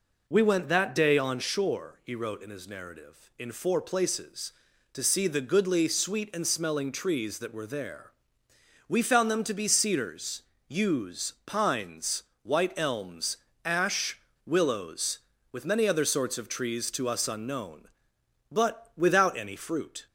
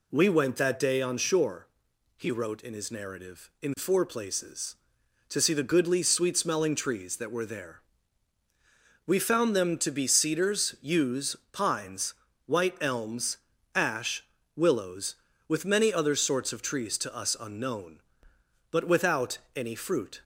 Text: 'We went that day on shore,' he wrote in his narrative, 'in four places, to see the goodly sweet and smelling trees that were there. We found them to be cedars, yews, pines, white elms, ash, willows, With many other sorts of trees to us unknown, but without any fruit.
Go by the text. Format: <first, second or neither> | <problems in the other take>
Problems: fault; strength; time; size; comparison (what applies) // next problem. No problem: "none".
first | skips "and"; at 6.3 s // pauses between "without" and "any"; slight; at 19.3 s; 0.16 s long